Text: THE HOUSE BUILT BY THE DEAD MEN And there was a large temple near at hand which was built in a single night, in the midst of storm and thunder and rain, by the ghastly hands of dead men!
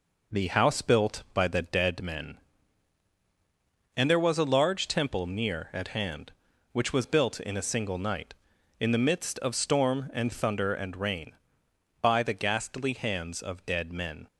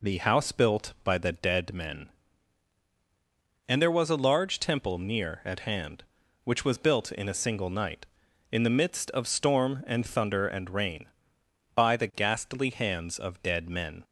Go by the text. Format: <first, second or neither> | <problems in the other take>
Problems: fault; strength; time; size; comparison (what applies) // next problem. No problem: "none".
second | gets quieter; noticeable; throughout; 4.5 dB